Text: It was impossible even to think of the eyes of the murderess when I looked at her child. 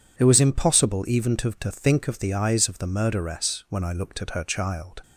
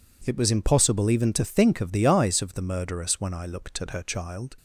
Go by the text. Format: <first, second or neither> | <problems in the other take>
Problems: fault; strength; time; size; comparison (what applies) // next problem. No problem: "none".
second | says "to" twice; at 1.5 s